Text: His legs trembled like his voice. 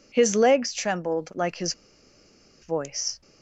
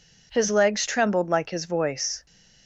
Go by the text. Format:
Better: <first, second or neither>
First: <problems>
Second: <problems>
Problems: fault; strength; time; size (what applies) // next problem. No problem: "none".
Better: second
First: pauses between "his" and "voice"; noticeable; at 1.7 s; 0.89 s long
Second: none